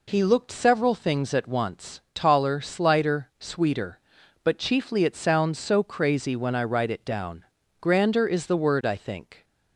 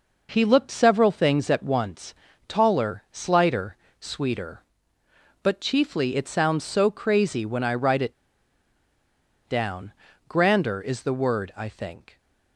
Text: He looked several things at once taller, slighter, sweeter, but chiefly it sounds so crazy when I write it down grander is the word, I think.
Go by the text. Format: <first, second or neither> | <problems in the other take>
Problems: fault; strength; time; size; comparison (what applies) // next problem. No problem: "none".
first | pauses between "once" and "taller"; slight; at 2.1 s; 0.32 s long // pauses between "it" and "down"; strong; at 8.1 s; 1.3 s long // pauses between "down" and "grander"; slight; at 9.9 s; 0.36 s long; slight in the first